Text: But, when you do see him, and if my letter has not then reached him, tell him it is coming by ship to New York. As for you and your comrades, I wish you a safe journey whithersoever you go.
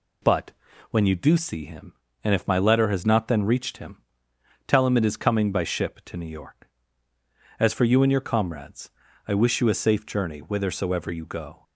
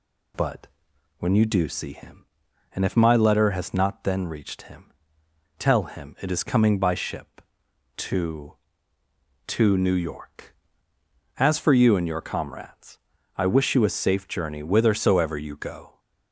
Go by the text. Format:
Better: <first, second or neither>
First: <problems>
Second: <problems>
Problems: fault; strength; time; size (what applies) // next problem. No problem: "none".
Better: first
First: none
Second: says "to" twice; at 9.4 s